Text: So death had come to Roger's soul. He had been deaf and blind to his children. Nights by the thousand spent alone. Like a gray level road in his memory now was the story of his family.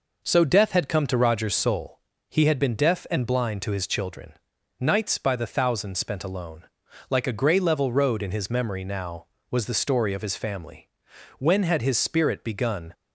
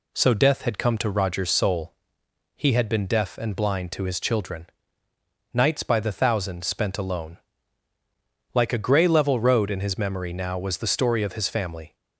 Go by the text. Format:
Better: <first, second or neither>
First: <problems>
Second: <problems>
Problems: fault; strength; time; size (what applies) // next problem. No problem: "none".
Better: second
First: goes on to say "When had his spirit begun"; from 11.3 s on; 1.5 s long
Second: none